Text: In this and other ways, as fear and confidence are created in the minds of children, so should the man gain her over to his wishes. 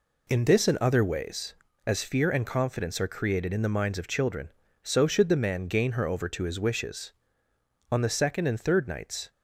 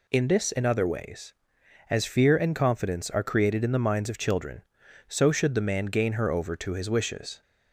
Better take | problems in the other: second | goes on to say "On the second and third nights"; from 7.9 s on; 1.4 s long

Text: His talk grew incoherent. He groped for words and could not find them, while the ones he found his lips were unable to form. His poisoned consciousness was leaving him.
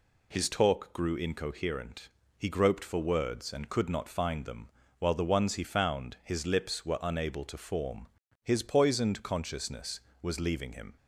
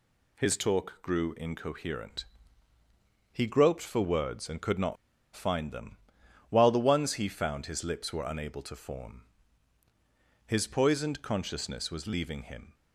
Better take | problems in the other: first | pauses between "not" and "find"; at 4.9 s; 0.39 s long

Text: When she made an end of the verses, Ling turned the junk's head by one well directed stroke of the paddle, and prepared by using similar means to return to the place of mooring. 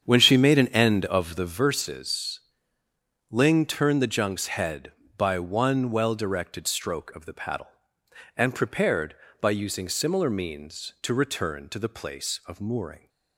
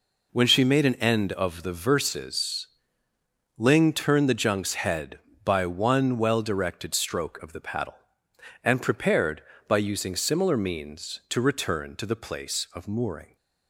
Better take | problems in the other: second | starts louder than the rest; strong; until 1.6 s; 8 dB

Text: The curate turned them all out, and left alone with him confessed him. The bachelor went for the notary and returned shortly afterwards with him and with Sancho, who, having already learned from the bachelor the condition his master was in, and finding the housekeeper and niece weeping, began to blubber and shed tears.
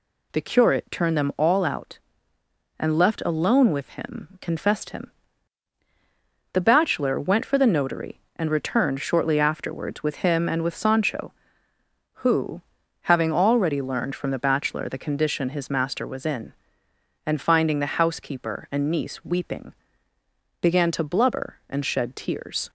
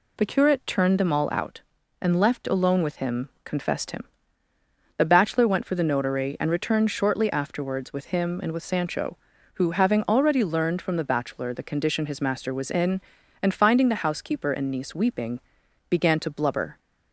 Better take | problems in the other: first | pauses between "him" and "confessed"; slight; at 3.2 s; 0.16 s long // stops before "and shed tears"; at 16.7 s

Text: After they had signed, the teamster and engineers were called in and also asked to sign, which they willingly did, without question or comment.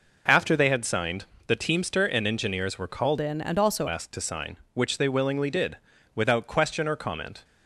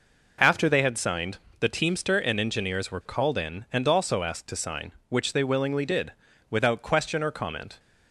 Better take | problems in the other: second | changes voice from "in" to "also"; from 3.2 to 3.8 s; 0.6 s long

